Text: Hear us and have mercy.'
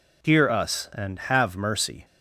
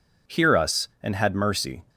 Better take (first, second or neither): first